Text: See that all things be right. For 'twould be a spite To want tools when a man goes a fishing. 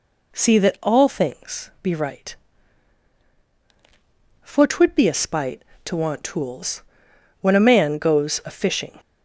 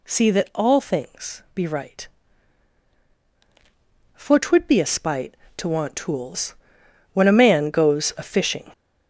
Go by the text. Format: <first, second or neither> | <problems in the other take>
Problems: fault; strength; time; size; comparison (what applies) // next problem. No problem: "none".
first | gets louder; noticeable; throughout; 5.5 dB // pauses between "tools" and "when"; noticeable; at 6.5 s; 0.58 s long; noticeable in the first